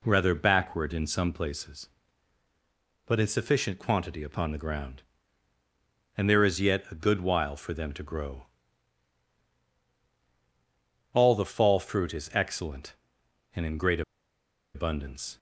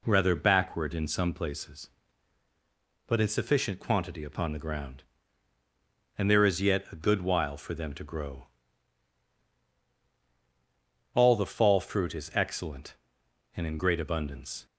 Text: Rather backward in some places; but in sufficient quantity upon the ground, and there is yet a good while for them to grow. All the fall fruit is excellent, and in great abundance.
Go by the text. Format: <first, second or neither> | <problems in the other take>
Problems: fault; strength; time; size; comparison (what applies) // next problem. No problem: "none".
second | pauses between "great" and "abundance"; noticeable; at 14.0 s; 0.73 s long